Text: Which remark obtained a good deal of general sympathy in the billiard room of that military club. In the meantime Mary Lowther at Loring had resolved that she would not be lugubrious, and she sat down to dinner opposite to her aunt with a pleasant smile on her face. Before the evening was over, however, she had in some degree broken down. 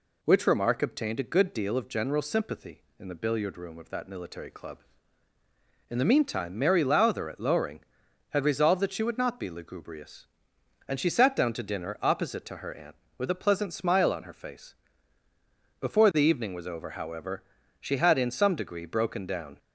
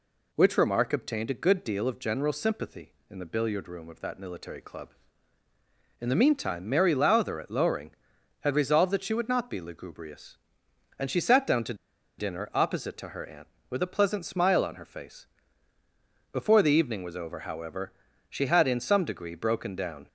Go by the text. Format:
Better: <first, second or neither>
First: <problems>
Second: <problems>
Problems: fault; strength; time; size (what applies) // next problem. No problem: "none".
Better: first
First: none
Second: pauses between "to" and "dinner"; at 11.7 s; 0.44 s long